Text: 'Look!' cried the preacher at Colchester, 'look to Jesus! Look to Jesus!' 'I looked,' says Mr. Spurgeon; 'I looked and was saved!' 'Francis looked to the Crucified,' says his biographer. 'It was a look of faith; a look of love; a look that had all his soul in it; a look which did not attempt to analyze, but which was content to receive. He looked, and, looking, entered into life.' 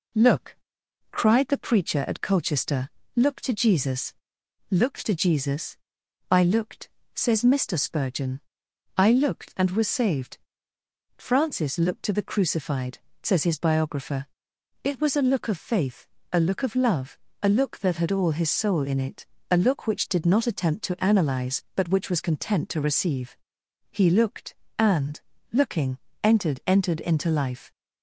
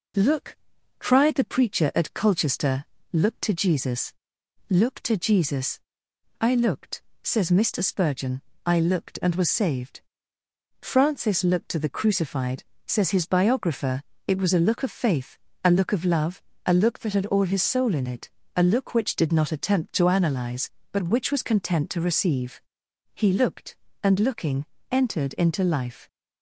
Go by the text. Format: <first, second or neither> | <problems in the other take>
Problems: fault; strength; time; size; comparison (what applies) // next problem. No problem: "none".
second | says "entered" twice; at 26.6 s